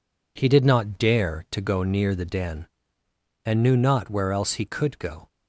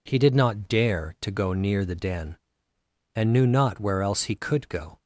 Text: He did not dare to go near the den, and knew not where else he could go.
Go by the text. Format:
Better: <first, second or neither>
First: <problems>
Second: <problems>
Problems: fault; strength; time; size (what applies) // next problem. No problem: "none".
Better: second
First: gets quieter; noticeable; throughout; 6 dB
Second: none